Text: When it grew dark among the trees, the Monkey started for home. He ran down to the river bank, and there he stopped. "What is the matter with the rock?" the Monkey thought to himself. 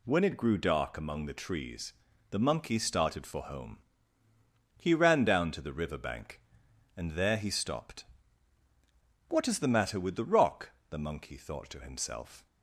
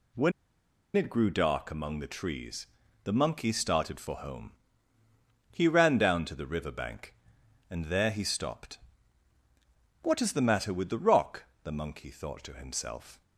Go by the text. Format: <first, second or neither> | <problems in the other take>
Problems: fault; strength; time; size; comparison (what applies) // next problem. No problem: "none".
first | pauses between "When" and "it"; noticeable; at 0.3 s; 0.65 s long